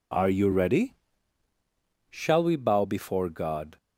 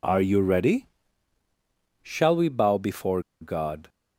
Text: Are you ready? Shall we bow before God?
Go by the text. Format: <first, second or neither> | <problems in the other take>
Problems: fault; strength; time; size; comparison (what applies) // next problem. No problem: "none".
first | pauses between "before" and "God"; slight; at 3.2 s; 0.18 s long